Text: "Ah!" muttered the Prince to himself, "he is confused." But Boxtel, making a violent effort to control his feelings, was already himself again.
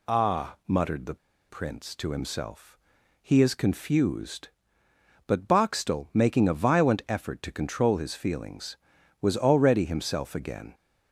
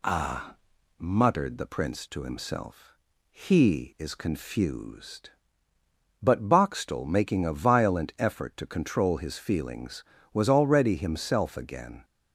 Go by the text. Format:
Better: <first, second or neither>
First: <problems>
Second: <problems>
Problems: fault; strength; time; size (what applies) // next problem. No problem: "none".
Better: second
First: pauses between "the" and "Prince"; slight; at 1.1 s; 0.33 s long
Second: none